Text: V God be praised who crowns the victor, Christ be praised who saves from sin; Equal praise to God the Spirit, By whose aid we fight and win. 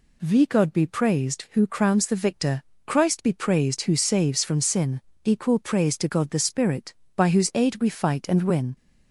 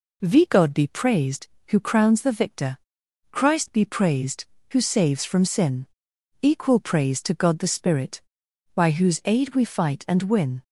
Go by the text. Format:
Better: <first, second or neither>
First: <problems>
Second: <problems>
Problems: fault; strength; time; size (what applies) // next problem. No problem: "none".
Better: neither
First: none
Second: none